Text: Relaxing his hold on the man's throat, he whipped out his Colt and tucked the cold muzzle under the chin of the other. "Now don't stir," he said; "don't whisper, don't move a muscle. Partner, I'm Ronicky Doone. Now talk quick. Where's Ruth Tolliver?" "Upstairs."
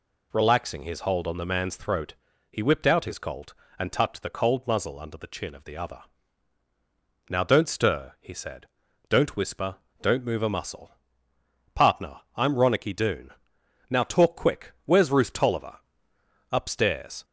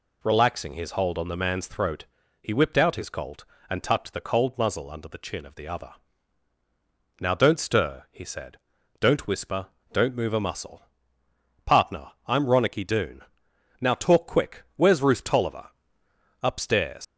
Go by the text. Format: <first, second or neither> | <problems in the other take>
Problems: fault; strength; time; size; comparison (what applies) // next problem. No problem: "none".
first | leaves "Upstairs" unfinished; at 17.0 s; 105 ms